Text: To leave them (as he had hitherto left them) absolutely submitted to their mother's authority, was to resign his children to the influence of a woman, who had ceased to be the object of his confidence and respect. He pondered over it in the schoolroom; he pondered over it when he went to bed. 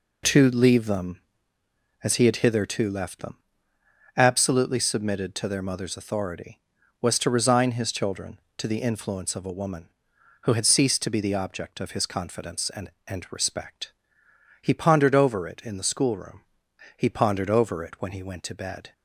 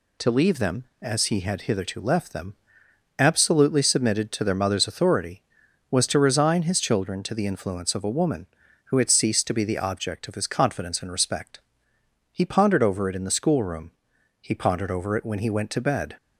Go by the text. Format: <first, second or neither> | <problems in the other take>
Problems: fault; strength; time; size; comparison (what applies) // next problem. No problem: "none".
second | says "and" twice; at 13.0 s